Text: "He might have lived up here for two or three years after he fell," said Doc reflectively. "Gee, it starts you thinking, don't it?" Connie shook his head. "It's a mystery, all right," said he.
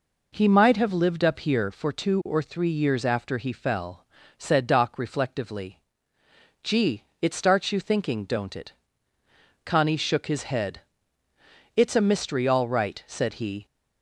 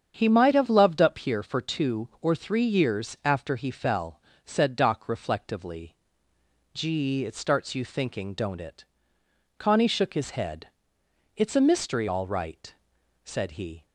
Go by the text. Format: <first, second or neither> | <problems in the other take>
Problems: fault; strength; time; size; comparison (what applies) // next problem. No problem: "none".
first | starts louder than the rest; strong; until 1.1 s; 8 dB // says "loved" for "lived"; at 0.6 s